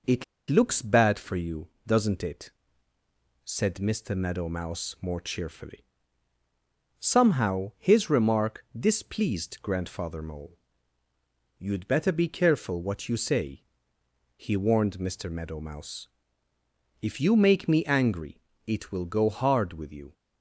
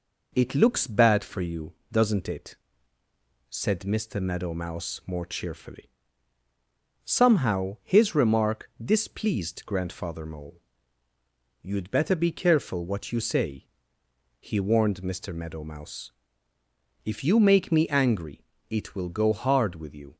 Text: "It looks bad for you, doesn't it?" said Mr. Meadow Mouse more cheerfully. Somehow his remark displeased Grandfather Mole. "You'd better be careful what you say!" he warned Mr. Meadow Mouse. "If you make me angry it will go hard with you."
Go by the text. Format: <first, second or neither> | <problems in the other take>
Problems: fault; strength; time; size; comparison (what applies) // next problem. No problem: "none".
second | pauses between "It" and "looks"; slight; at 0.2 s; 0.24 s long // pauses between "angry" and "it"; slight; at 18.4 s; 0.24 s long; slight in the second